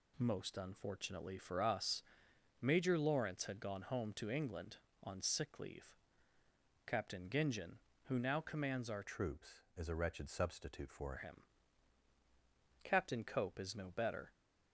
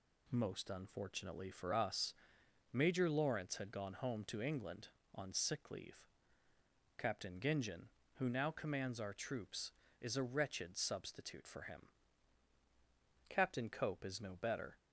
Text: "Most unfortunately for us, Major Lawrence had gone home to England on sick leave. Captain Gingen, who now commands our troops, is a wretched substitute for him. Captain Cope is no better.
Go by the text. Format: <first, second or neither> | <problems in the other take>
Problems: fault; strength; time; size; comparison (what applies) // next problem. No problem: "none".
second | changes voice from "troops" to "for"; from 9.0 to 11.1 s; 2.1 s long